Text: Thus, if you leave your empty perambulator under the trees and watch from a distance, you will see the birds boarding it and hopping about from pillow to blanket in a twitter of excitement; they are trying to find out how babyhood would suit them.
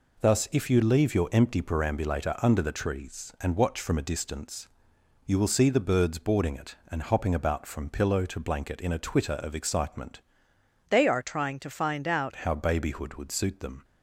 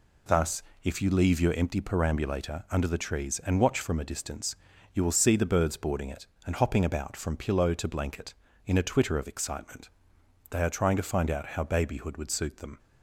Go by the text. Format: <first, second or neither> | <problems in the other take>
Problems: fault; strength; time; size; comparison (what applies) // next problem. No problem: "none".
second | changes voice from "they" to "out"; from 10.8 to 12.3 s; 1.5 s long